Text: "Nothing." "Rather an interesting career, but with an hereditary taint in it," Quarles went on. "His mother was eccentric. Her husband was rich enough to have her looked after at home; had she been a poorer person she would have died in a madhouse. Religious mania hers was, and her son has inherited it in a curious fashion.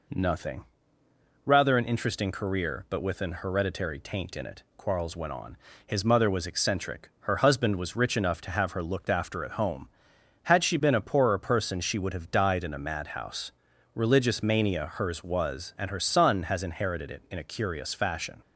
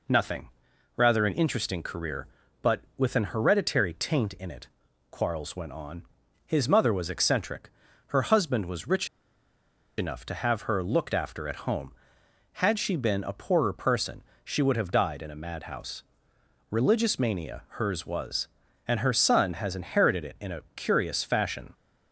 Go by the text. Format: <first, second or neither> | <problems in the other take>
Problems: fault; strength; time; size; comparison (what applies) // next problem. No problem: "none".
first | pauses between "rich" and "enough"; noticeable; at 9.0 s; 0.91 s long // pauses between "person" and "she"; slight; at 14.2 s; 0.22 s long // pauses between "a" and "curious"; slight; at 20.6 s; 0.16 s long